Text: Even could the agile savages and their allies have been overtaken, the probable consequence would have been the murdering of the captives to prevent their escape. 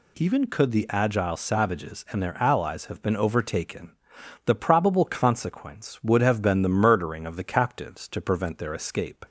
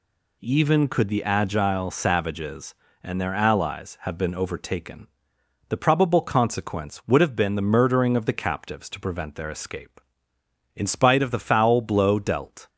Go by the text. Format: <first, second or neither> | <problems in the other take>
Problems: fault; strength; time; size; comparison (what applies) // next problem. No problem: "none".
first | goes on to say "In spite of the foul blow dealt"; strong; from 10.7 s on; 1.9 s long